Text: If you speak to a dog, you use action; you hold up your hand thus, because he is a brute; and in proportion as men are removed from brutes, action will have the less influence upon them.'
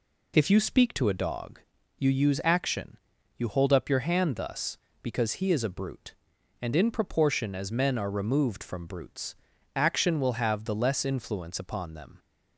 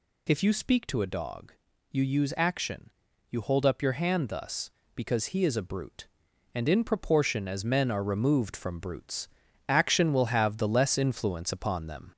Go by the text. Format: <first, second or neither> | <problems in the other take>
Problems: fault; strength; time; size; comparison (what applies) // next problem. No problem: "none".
first | gets louder; slight; throughout; 2.5 dB